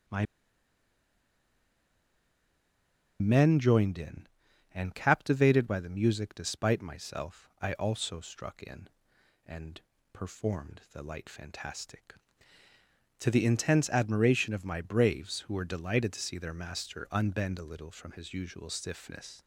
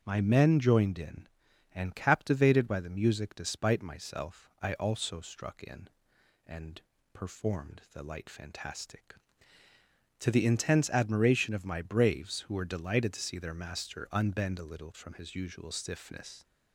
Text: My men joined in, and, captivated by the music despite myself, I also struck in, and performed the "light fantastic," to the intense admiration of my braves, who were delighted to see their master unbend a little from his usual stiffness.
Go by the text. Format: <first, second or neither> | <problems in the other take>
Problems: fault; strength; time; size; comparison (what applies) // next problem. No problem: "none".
second | starts louder than the rest; strong; until 4.0 s; 7 dB; strong in the second // pauses between "My" and "men"; strong; at 0.2 s; 2.9 s long // pauses between "and" and "performed"; slight; at 9.8 s; 0.32 s long; slight in the second